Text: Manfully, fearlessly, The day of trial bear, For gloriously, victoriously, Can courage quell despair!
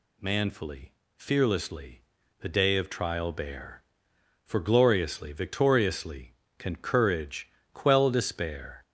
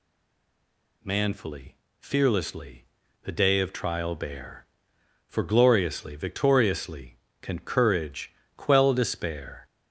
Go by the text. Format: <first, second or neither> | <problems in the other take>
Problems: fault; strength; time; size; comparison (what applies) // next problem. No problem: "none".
first | stays silent before the first word; until 1.0 s; 1.0 s long // pauses between "courage" and "quell"; slight; at 8.3 s; 0.20 s long; slight in the first